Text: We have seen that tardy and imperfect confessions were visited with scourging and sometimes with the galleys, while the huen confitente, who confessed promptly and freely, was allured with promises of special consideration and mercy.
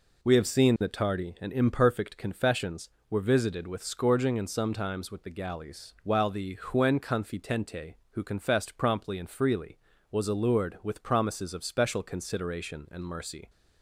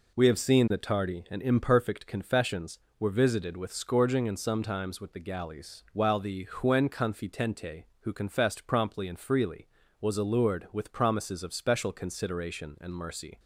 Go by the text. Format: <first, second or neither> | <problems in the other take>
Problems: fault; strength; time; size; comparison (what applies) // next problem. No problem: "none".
neither | none